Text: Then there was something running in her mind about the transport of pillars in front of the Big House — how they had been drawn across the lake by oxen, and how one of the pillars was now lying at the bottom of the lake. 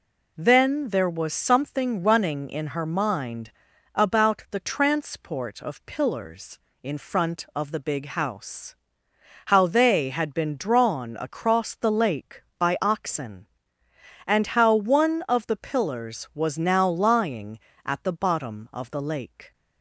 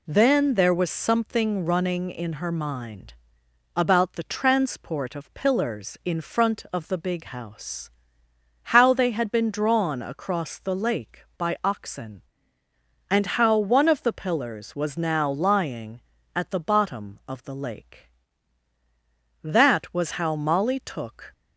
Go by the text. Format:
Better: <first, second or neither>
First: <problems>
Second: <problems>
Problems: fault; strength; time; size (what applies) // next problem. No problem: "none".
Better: first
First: pauses between "mind" and "about"; at 3.5 s; 0.42 s long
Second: pauses between "mind" and "about"; noticeable; at 3.1 s; 0.62 s long // goes on to say "That was how Molly took"; strong; from 19.4 s on; 1.8 s long